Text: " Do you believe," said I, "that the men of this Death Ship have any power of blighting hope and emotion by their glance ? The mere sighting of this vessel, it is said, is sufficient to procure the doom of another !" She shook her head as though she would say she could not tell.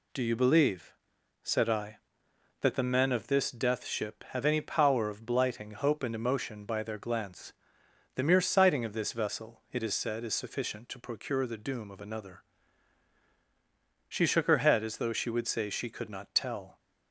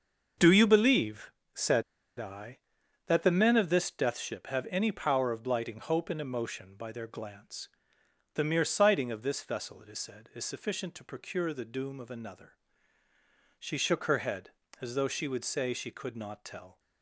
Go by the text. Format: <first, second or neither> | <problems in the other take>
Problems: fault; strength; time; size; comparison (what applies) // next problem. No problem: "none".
first | starts louder than the rest; until 1.5 s; 6.5 dB // pauses between "said" and "I"; at 1.8 s; 0.36 s long